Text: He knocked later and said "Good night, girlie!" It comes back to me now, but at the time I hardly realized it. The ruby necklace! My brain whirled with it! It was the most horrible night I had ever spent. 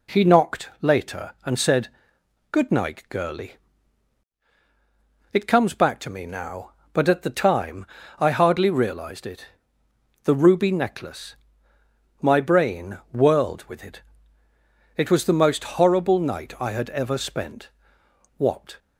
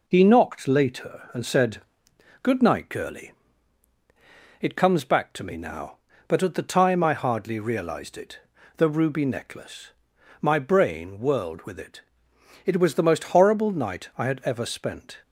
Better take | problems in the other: second | pauses between "said" and "Good"; noticeable; at 1.8 s; 0.60 s long; noticeable in the second // pauses between "time" and "I"; slight; at 7.8 s; 0.33 s long // pauses between "brain" and "whirled"; slight; at 12.9 s; 0.16 s long // goes on to say "What"; slight; from 18.3 s on; 0.40 s long

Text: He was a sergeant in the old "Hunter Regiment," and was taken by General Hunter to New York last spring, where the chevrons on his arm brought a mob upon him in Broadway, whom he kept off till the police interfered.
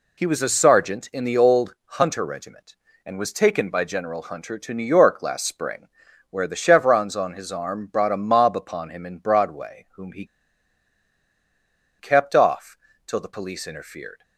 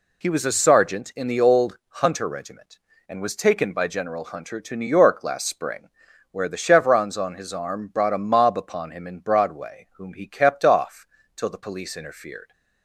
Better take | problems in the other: second | pauses between "he" and "kept"; strong; at 10.2 s; 1.7 s long // pauses between "off" and "till"; slight; at 12.7 s; 0.30 s long; slight in the second

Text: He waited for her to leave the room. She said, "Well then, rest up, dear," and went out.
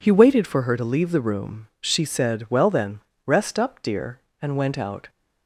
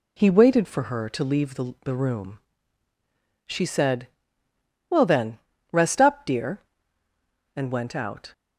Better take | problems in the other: first | says "the" twice; at 1.8 s

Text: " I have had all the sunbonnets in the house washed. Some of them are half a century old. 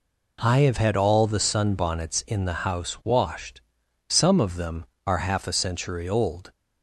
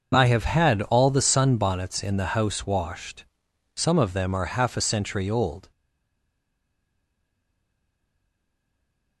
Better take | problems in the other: first | starts louder than the rest; until 1.1 s; 6 dB // stays silent after the last word; strong; from 5.7 s on; 3.5 s long

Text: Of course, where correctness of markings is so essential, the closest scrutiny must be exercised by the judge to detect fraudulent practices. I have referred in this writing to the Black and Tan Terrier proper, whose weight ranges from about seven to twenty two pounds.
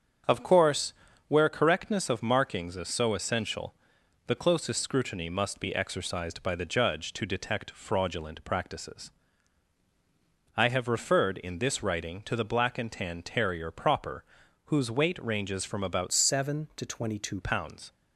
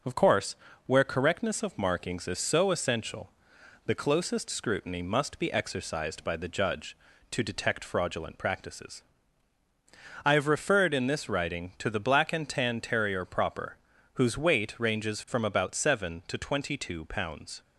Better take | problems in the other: second | starts louder than the rest; strong; until 1.6 s; 7.5 dB // changes voice from "seven" to "two"; from 16.1 to 17.4 s; 1.3 s long

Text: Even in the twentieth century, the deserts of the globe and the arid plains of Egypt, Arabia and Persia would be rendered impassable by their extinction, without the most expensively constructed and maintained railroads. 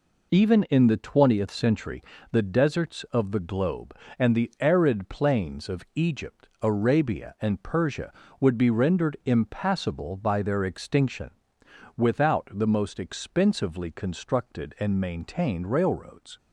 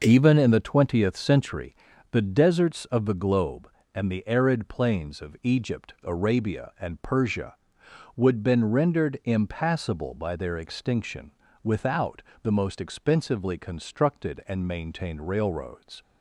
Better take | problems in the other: first | starts louder than the rest; noticeable; until 1.0 s; 6 dB // says "been" for "be"; at 8.4 s // pauses between "without" and "the"; slight; at 12.2 s; 0.18 s long

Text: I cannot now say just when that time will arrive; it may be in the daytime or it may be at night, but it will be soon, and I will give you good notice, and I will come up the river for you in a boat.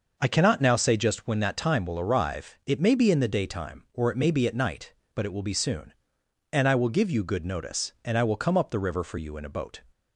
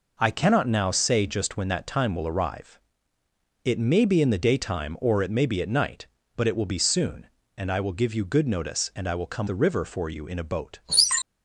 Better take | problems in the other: first | skips "up"; at 9.4 s

